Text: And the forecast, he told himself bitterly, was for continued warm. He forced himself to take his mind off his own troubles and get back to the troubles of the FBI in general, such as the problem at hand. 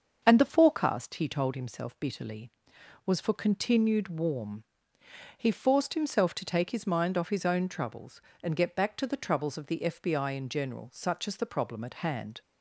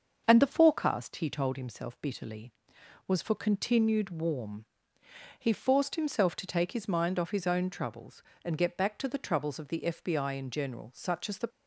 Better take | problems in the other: first | starts louder than the rest; until 1.2 s; 6.5 dB; also in the first // stops before "problem at hand"; at 11.4 s

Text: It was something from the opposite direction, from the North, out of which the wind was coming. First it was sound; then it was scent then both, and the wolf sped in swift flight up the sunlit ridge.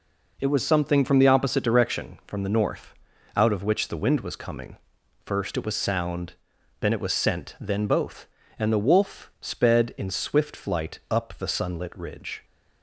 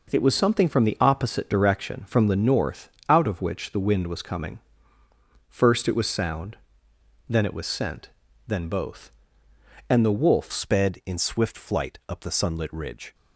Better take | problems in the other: first | pauses between "scent" and "then"; at 8.0 s; 0.38 s long // changes voice at "sped"; from 10.5 s on; 2.6 s long

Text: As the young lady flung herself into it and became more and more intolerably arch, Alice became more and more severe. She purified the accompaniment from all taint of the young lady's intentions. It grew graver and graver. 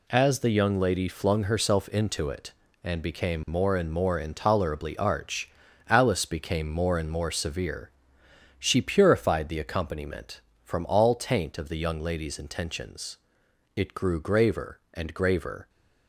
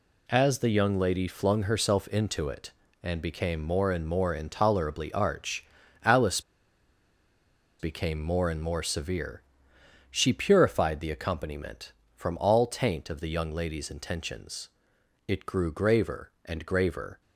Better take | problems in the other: first | pauses between "Alice" and "became"; strong; at 6.4 s; 1.3 s long

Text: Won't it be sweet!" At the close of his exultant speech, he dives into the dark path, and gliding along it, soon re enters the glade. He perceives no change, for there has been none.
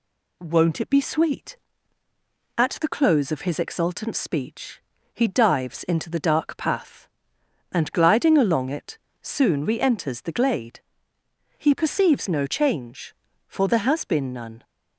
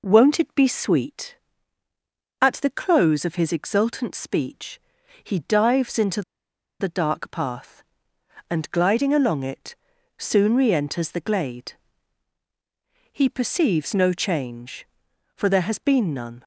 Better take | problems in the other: first | pauses between "into" and "the"; noticeable; at 6.2 s; 0.59 s long

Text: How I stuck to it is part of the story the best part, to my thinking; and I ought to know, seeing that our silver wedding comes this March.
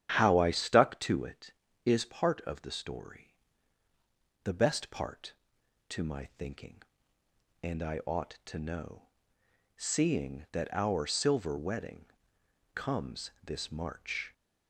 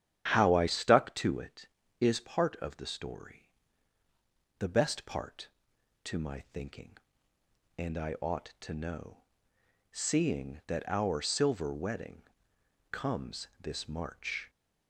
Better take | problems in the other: neither | starts louder than the rest; strong; the same in both // pauses between "story" and "the"; the same in both // pauses between "wedding" and "comes"; noticeable; the same in both

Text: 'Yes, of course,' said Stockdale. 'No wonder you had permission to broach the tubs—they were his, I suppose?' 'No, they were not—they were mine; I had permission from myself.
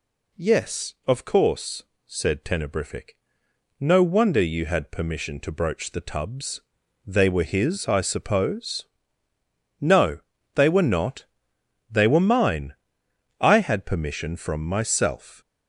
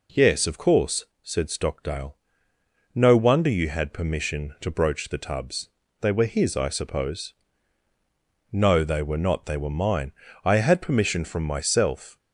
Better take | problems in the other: second | says "Tenebrific" for "Stockdale"; at 2.4 s

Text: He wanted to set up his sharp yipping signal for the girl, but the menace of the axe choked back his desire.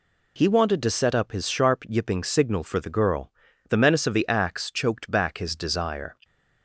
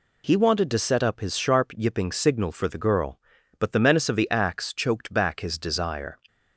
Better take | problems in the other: second | skips "but"; at 3.5 s

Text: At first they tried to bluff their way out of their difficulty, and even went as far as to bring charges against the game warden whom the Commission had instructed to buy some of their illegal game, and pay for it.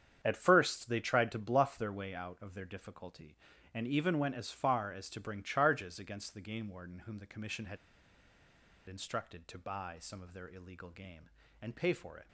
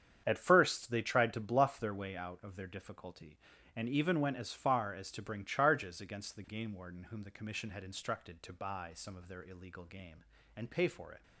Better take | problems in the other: second | starts louder than the rest; strong; until 1.2 s; 8 dB; strong in the second // pauses between "had" and "instructed"; at 7.7 s; 1.1 s long

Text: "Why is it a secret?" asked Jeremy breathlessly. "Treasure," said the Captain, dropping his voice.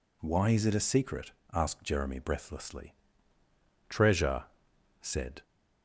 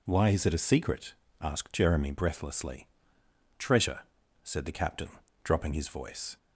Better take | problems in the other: second | stops before "the Captain dropping his voice"; at 5.4 s

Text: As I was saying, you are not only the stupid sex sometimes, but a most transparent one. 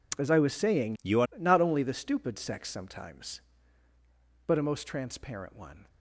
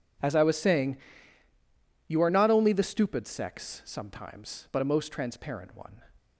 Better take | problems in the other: second | changes voice from "you" to "are"; from 1.0 to 1.2 s; 0.2 s long

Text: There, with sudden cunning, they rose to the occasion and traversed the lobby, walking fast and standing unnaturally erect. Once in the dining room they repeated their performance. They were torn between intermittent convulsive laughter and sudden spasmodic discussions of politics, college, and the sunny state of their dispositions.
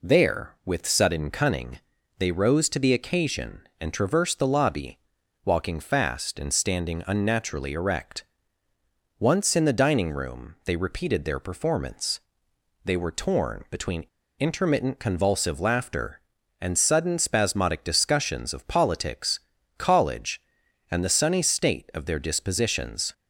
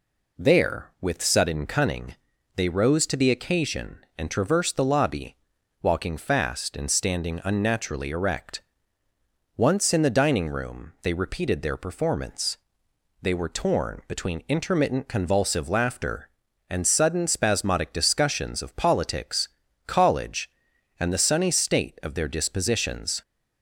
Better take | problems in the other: second | pauses between "between" and "intermittent"; slight; at 14.0 s; 0.32 s long

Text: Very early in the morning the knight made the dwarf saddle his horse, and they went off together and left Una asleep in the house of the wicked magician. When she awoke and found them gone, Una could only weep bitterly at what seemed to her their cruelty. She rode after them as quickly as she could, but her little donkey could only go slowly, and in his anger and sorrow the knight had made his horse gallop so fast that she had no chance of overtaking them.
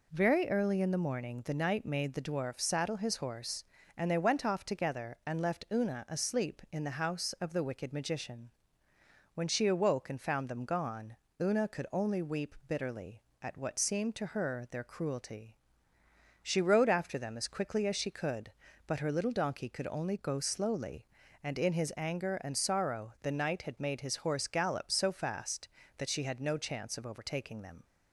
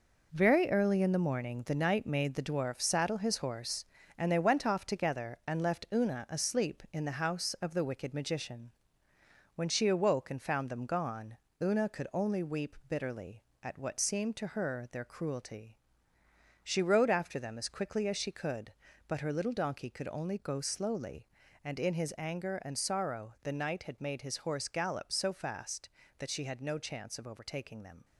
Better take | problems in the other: first | gets quieter; strong; throughout; 8.5 dB

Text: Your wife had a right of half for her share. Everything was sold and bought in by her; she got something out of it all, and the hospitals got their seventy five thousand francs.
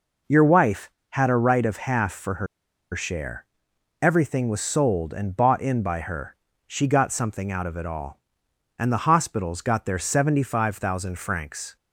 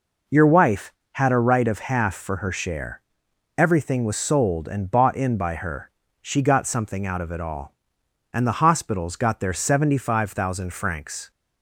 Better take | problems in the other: second | pauses between "her" and "share"; noticeable; at 2.4 s; 0.47 s long

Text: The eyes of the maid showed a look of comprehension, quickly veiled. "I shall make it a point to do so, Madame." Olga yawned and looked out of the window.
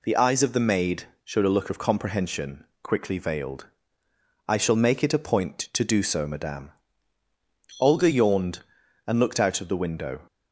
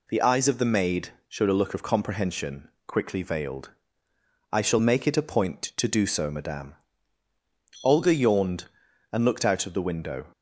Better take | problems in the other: neither | pauses between "maid" and "showed"; slight; the same in both

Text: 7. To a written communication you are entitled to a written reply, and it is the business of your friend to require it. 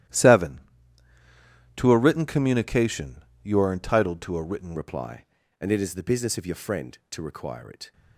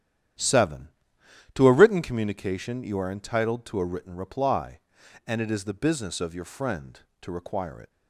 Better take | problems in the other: second | starts louder than the rest; strong; until 2.2 s; 13 dB; strong in the second // pauses between "communication" and "you"; slight; at 3.1 s; 0.26 s long // changes voice at "reply"; from 4.7 s on; 3.2 s long

